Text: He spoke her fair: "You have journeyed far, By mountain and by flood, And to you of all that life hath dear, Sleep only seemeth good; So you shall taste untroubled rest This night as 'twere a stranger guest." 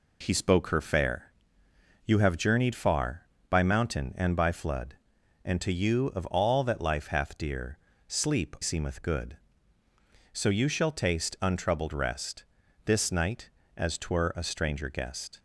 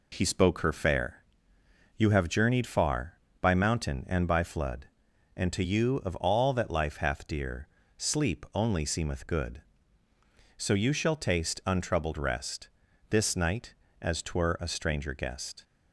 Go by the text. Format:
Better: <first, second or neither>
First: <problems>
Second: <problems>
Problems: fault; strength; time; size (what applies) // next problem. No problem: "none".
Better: second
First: skips "only"; at 8.5 s // pauses between "rest" and "This"; at 12.4 s; 0.42 s long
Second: pauses between "rest" and "This"; at 12.6 s; 0.42 s long